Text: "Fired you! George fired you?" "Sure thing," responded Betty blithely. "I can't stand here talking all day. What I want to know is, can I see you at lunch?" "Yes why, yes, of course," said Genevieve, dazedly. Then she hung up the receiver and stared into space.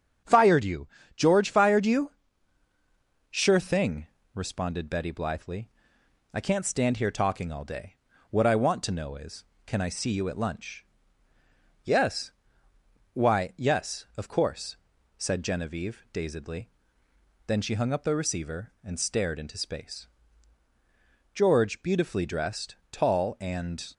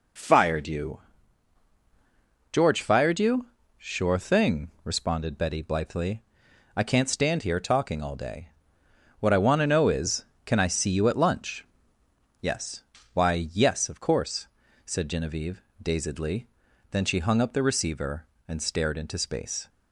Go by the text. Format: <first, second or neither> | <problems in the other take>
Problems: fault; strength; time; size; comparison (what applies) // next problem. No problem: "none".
second | starts louder than the rest; strong; until 1.5 s; 7.5 dB // pauses between "Yes" and "why"; noticeable; at 12.3 s; 0.84 s long; slight in the second // goes on to say "George beautifully dressed tall and"; strong; from 21.3 s on; 2.5 s long